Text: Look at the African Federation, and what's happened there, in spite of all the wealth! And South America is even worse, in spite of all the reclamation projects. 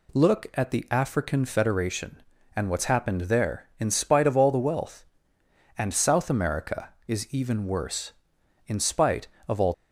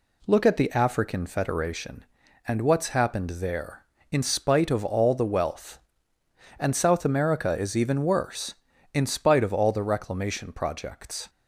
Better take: second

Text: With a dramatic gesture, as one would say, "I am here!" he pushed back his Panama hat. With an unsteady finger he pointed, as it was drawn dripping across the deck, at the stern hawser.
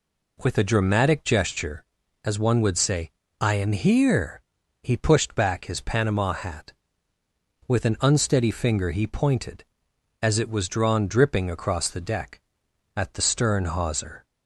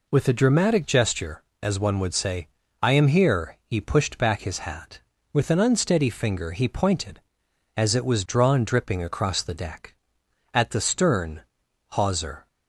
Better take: first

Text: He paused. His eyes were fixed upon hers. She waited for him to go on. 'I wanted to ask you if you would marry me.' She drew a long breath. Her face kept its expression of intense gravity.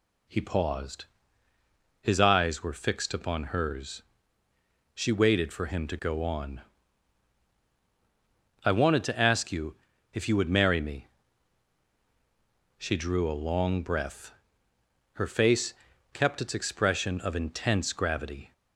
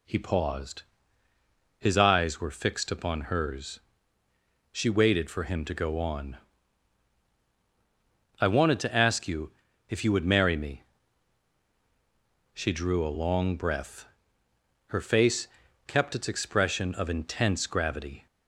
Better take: neither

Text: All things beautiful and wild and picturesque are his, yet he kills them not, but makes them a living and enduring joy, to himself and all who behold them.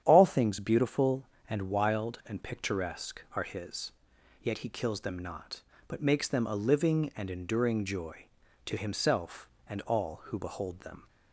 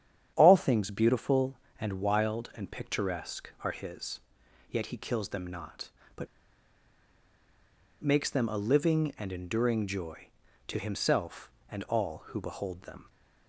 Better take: first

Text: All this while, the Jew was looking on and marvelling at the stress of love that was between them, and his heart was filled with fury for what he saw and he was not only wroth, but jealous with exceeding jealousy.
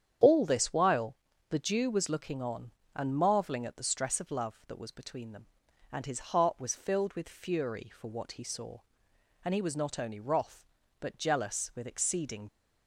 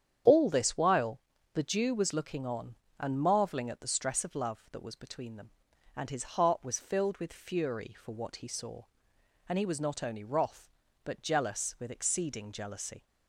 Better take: second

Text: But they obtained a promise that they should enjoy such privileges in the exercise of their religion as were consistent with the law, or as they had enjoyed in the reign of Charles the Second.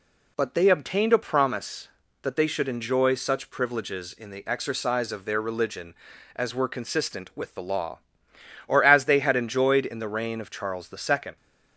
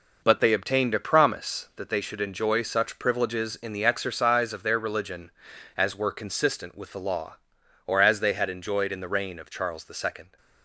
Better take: first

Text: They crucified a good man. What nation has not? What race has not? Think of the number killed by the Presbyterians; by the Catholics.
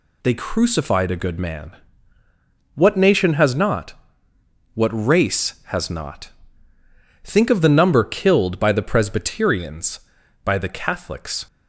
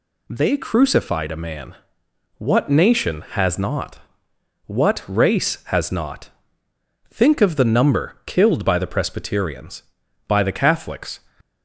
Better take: first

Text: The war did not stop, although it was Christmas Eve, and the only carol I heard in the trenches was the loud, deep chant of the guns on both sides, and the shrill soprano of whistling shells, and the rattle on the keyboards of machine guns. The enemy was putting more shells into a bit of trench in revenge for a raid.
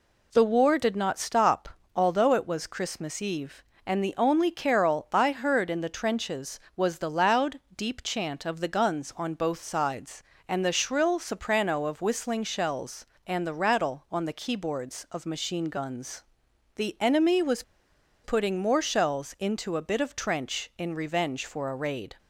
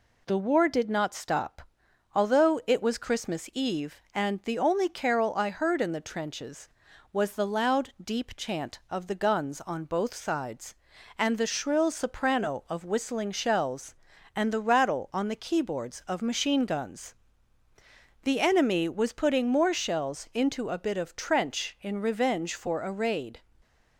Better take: second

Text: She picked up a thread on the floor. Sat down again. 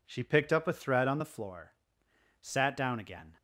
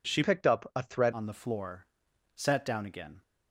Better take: first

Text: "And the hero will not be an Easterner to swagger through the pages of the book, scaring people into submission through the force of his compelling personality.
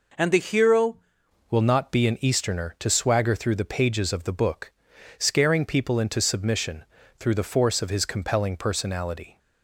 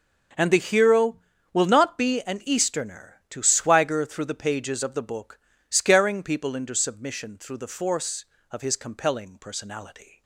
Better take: second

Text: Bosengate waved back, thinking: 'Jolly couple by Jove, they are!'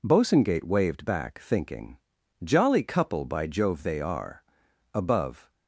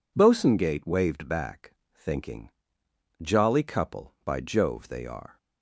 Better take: second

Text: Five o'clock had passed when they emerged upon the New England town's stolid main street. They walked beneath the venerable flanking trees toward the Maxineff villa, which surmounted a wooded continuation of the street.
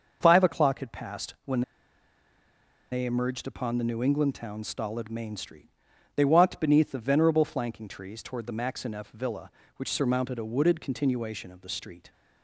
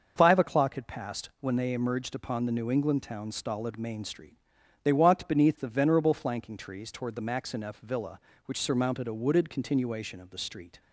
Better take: second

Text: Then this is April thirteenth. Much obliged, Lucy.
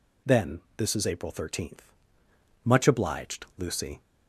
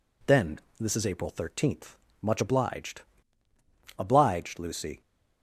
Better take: first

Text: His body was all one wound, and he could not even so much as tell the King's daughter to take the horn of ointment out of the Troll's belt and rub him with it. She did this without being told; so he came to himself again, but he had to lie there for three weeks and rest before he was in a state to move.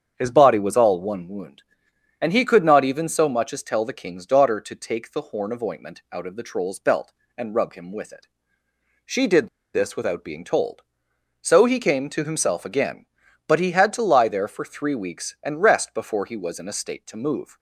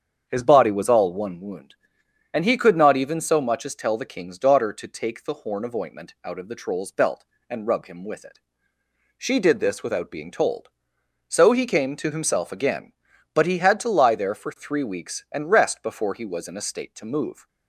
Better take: second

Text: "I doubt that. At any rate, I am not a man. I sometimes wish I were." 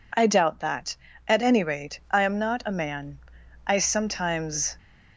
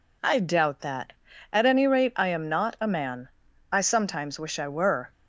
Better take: second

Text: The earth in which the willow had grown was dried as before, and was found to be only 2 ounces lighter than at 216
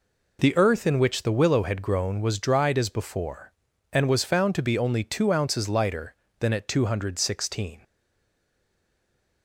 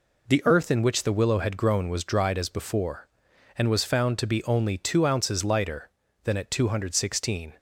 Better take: second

